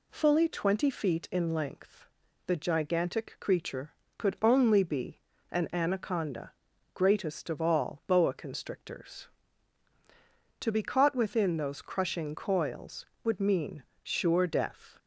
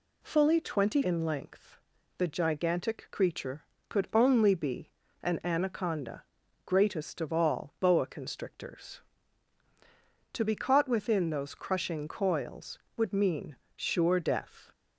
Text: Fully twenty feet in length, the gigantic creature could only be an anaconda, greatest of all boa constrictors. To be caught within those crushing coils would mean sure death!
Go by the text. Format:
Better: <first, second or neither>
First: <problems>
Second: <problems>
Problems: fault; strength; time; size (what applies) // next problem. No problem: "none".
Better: first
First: pauses between "be" and "an"; slight; at 5.2 s; 0.30 s long // pauses between "mean" and "sure"; slight; at 13.8 s; 0.20 s long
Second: skips "feet"; at 1.0 s // pauses between "be" and "an"; slight; at 4.9 s; 0.30 s long // pauses between "mean" and "sure"; slight; at 13.5 s; 0.20 s long